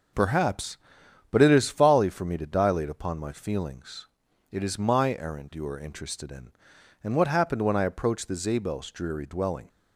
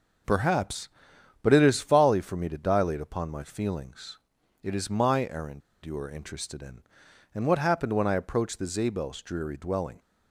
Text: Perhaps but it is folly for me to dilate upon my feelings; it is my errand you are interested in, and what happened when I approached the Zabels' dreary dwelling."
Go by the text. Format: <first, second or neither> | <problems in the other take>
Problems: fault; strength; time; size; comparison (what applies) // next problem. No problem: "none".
first | starts louder than the rest; until 1.8 s; 6 dB; also in the first // pauses between "errand" and "you"; slight; at 5.6 s; 0.24 s long